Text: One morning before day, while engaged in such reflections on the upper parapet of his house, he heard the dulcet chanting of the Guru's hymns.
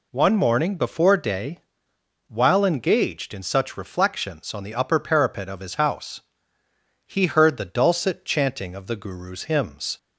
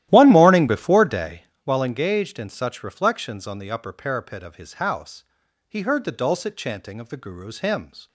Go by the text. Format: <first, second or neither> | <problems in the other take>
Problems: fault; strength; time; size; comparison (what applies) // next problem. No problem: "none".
first | starts louder than the rest; strong; until 1.6 s; 14 dB